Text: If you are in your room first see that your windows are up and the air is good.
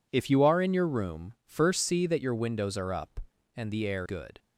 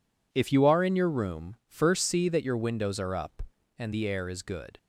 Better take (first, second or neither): second